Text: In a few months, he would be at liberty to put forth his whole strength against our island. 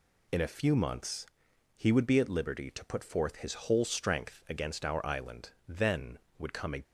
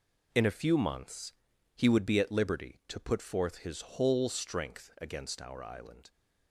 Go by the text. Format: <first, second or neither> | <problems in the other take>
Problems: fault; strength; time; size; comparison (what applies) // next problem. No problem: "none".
second | goes on to say "Then would come a"; noticeable; from 5.6 s on; 1.1 s long